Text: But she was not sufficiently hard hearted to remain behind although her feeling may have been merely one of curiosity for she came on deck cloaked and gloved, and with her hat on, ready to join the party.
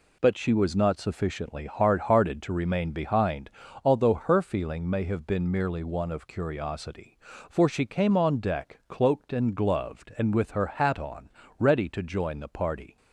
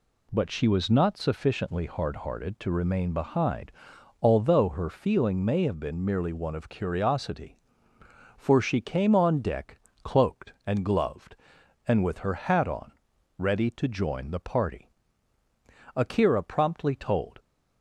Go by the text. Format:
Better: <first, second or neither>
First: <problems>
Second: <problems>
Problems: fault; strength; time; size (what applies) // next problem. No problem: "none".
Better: first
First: pauses between "behind" and "although"; slight; at 3.5 s; 0.34 s long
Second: pauses between "behind" and "although"; noticeable; at 3.7 s; 0.50 s long // pauses between "deck" and "cloaked"; slight; at 9.7 s; 0.24 s long // goes on to say "Akira promptly told"; from 15.9 s on; 1.4 s long